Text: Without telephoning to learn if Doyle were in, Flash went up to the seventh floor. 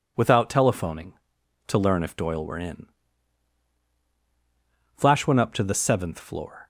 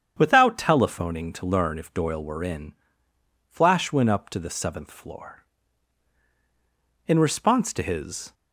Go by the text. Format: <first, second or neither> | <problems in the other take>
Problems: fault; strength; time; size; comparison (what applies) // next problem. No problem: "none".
first | starts louder than the rest; strong; until 1.1 s; 8 dB // goes on to say "In response to his"; noticeable; from 7.0 s on; 1.2 s long